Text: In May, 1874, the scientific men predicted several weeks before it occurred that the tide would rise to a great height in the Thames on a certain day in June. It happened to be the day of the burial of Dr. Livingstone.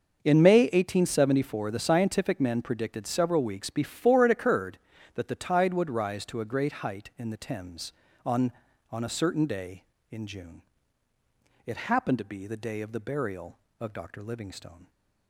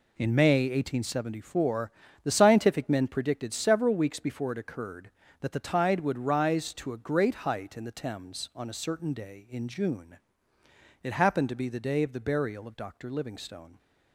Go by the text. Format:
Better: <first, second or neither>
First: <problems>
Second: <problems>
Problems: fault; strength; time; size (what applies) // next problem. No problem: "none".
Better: second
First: starts louder than the rest; until 1.2 s; 6 dB // says "on" twice; at 8.9 s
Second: none